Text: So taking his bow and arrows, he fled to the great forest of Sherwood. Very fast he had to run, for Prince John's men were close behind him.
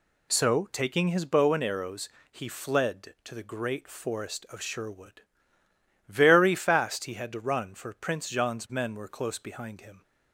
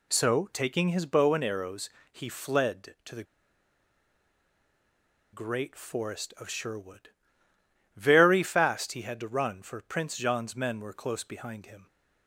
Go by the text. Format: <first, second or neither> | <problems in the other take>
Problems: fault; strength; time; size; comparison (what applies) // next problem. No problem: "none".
first | pauses between "the" and "great"; strong; at 3.2 s; 2.0 s long